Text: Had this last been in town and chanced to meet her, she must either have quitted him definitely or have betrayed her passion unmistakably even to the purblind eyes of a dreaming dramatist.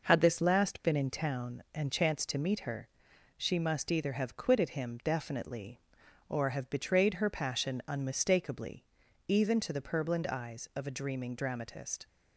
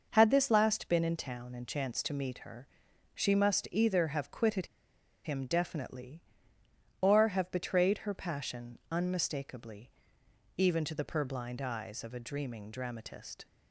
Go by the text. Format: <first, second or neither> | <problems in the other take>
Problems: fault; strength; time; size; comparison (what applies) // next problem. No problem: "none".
first | pauses between "quitted" and "him"; noticeable; at 4.6 s; 0.57 s long // pauses between "unmistakably" and "even"; noticeable; at 9.9 s; 0.68 s long; also in the first